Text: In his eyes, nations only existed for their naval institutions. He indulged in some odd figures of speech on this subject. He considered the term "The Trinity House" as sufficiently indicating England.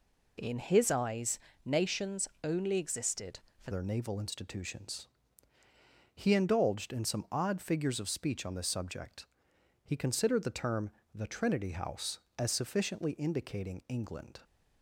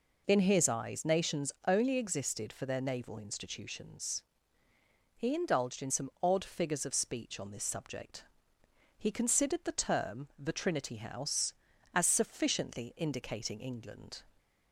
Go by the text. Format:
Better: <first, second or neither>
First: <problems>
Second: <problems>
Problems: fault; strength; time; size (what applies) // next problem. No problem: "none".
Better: second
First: pauses between "nations" and "only"; slight; at 2.2 s; 0.16 s long // changes voice at "their"; from 3.7 s on; 10.7 s long // pauses between "term" and "The"; slight; at 10.9 s; 0.24 s long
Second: none